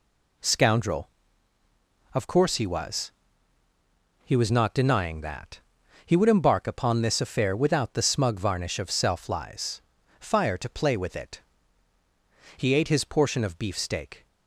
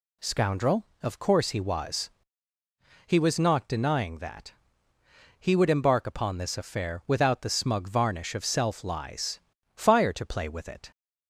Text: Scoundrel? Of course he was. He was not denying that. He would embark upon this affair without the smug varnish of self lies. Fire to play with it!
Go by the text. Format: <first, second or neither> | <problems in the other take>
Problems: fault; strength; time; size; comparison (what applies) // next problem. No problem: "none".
second | goes on to say "He ate his portion of beefsteak"; strong; from 12.5 s on; 1.6 s long